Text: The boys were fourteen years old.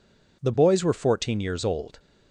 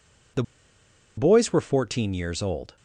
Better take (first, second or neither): first